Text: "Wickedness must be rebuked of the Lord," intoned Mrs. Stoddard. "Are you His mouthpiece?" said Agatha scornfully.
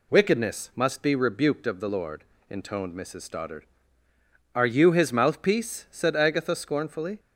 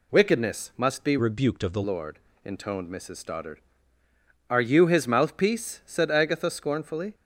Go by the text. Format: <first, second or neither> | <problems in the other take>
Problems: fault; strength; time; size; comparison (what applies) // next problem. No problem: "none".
first | changes voice from "rebuked" to "the"; from 1.1 to 1.8 s; 0.7 s long